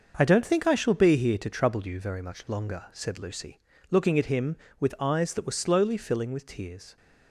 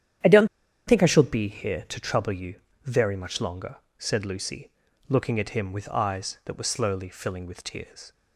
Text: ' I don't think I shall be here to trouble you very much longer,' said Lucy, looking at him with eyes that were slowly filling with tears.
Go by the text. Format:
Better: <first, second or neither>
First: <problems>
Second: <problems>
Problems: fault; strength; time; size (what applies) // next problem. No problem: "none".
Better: first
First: starts louder than the rest; noticeable; until 1.1 s; 6 dB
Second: starts louder than the rest; strong; until 1.6 s; 10.5 dB // pauses between "don't" and "think"; at 0.4 s; 0.41 s long // pauses between "you" and "very"; slight; at 2.5 s; 0.30 s long